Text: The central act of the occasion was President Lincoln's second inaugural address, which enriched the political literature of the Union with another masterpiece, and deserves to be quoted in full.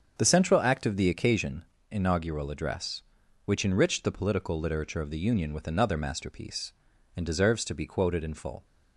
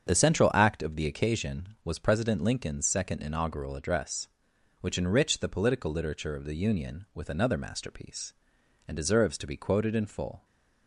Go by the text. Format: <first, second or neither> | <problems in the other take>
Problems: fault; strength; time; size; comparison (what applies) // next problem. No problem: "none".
second | starts louder than the rest; until 1.1 s; 7 dB; strong in the second // skips "was President Lincoln's second"; at 1.7 s